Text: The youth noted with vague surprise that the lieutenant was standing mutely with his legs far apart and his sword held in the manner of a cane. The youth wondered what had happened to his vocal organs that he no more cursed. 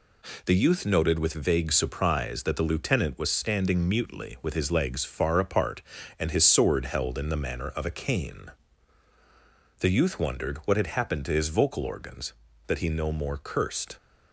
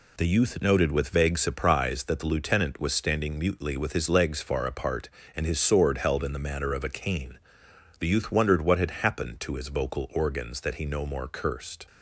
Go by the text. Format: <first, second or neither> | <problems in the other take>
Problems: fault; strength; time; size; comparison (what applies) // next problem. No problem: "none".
neither | none